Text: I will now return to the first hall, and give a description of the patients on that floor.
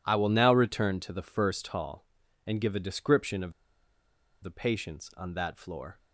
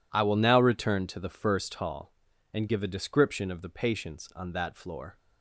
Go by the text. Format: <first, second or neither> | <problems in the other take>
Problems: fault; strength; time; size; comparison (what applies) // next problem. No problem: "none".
second | pauses between "of" and "the"; noticeable; at 3.5 s; 0.89 s long